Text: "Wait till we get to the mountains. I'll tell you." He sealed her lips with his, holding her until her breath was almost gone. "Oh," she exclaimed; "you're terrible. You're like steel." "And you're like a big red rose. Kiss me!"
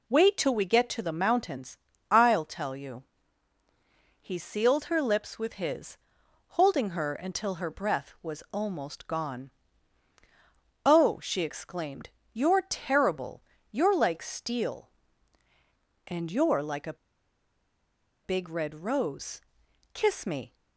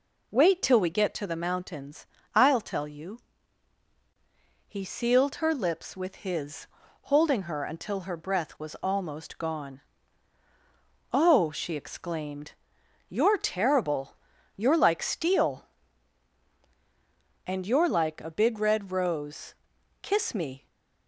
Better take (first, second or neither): second